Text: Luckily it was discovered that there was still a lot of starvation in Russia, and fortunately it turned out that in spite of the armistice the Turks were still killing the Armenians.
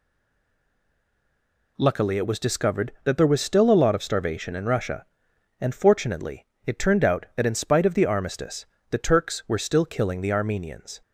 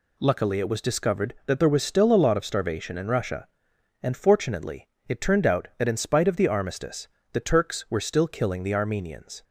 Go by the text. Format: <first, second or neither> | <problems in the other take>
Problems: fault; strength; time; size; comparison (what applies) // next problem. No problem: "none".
second | stays silent before the first word; noticeable; until 1.7 s; 1.7 s long // pauses between "fortunately" and "it"; slight; at 6.4 s; 0.20 s long; slight in the second // pauses between "armistice" and "the"; slight; at 8.6 s; 0.26 s long; slight in the second